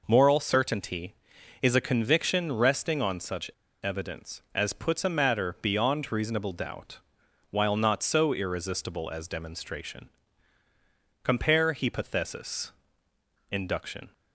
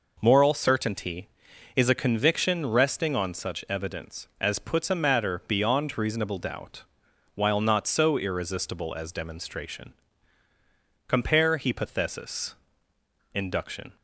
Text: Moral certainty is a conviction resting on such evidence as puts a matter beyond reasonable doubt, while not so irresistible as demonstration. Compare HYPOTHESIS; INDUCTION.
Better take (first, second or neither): second